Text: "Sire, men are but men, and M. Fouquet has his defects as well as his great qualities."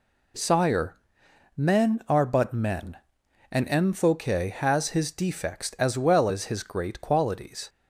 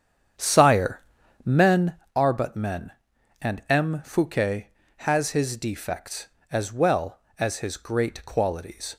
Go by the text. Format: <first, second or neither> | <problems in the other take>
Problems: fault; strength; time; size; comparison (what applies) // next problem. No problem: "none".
first | starts louder than the rest; strong; until 2.1 s; 8.5 dB